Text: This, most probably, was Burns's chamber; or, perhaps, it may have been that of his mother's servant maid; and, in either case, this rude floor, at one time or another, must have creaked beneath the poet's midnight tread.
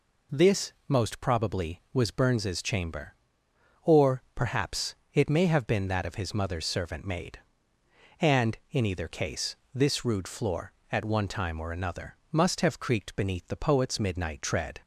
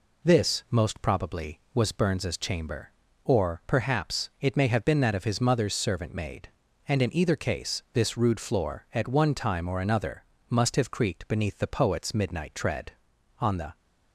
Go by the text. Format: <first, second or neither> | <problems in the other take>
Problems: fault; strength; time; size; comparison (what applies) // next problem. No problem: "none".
first | goes on to say "On the"; slight; from 13.3 s on; 0.38 s long